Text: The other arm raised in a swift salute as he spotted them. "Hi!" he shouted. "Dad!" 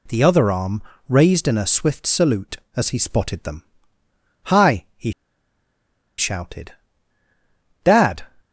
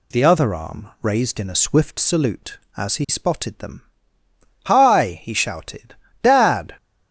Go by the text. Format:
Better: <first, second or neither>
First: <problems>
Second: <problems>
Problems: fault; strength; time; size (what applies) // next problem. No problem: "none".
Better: second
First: pauses between "arm" and "raised"; slight; at 0.8 s; 0.26 s long // pauses between "he" and "shouted"; at 5.1 s; 1.0 s long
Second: none